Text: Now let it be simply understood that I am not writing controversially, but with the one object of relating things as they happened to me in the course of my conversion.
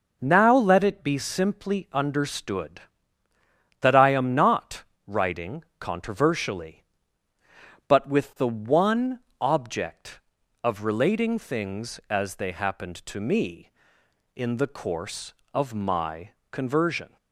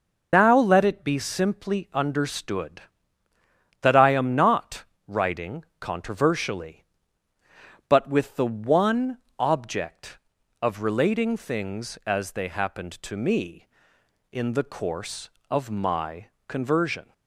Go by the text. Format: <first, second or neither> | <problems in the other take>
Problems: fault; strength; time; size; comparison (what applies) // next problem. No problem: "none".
first | loses the start of "Now"; at 0.3 s; 110 ms // pauses between "not" and "writing"; slight; at 4.8 s; 0.24 s long; slight in the first // pauses between "one" and "object"; slight; at 9.1 s; 0.22 s long; slight in the first // pauses between "my" and "conversion"; slight; at 16.2 s; 0.22 s long; slight in the first